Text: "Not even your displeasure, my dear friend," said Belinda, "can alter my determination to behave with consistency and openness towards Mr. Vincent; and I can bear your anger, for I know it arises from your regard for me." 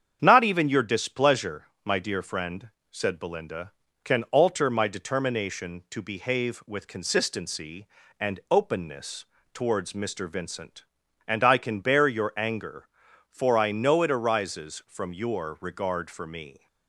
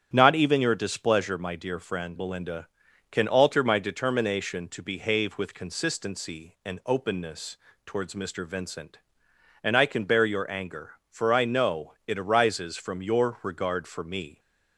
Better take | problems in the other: first | starts louder than the rest; strong; until 1.1 s; 9 dB; strong in the first // skips "said"; at 2.1 s // pauses between "openness" and "towards"; slight; at 7.5 s; 0.30 s long; slight in the first

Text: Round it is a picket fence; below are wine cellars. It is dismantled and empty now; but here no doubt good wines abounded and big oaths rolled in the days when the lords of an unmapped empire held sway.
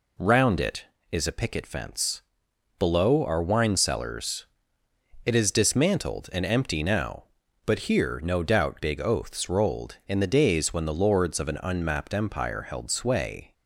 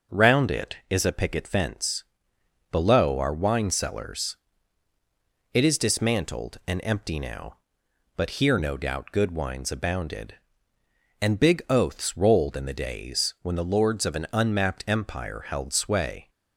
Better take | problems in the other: second | skips "good wines abounded and"; at 8.8 s

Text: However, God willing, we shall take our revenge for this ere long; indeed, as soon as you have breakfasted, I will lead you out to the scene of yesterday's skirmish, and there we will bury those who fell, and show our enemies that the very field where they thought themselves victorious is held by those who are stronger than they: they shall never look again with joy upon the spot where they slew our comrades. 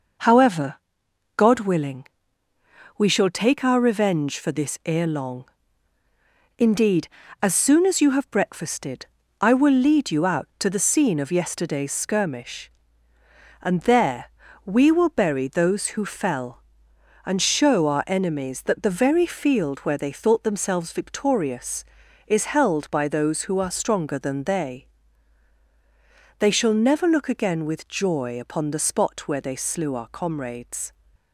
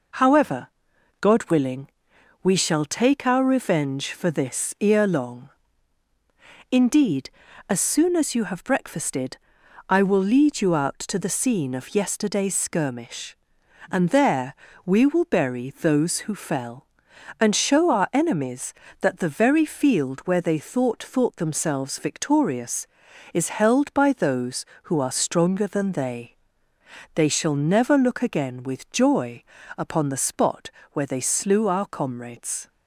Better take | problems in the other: first | pauses between "there" and "we"; slight; at 14.5 s; 0.28 s long; slight in the first // says "thought" twice; at 21.0 s // pauses between "joy" and "upon"; slight; at 29.4 s; 0.32 s long // pauses between "spot" and "where"; slight; at 30.6 s; 0.24 s long

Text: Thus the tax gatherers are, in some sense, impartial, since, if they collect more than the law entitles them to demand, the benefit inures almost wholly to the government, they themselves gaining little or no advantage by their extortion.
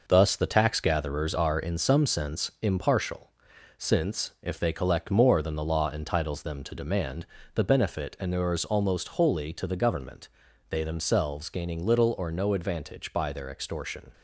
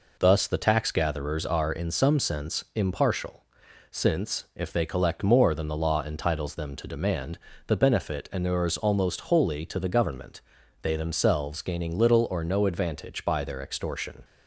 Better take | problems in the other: second | gets quieter; throughout; 6.5 dB

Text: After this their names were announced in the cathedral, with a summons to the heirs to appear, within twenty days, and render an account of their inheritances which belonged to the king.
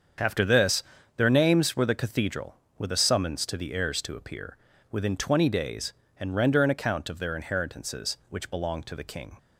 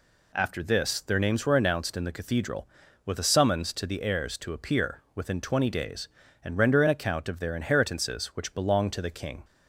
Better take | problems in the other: second | starts louder than the rest; strong; until 1.5 s; 7.5 dB // pauses between "this" and "their"; slight; at 0.8 s; 0.34 s long // skips "announced in"; at 1.8 s

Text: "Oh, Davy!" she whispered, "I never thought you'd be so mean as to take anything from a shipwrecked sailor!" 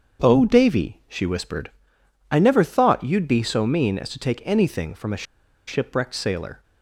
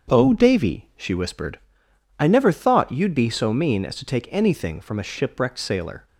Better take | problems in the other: second | starts louder than the rest; strong; until 1.3 s; 7 dB; strong in the second // pauses between "a" and "shipwrecked"; at 5.2 s; 0.44 s long

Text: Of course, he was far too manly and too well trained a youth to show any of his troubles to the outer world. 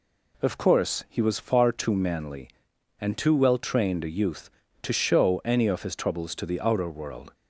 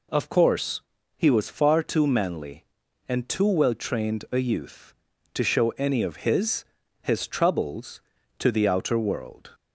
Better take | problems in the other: first | says "his" twice; at 7.0 s

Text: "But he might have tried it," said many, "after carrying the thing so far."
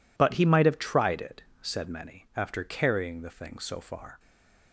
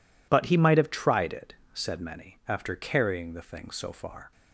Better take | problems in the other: second | stays silent after the last word; slight; from 4.1 s on; 0.6 s long

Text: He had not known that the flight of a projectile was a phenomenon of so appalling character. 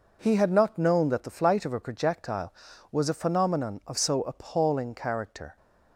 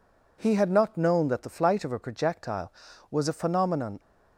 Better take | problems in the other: first | stops before "of so appalling character"; at 3.9 s

